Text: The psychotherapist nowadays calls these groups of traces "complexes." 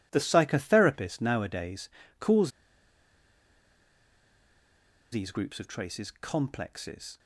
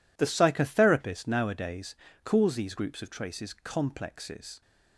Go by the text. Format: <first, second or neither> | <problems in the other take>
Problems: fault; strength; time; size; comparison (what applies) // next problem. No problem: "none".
second | pauses between "nowadays" and "calls"; slight; at 1.8 s; 0.32 s long; slight in the second // pauses between "calls" and "these"; strong; at 2.5 s; 2.6 s long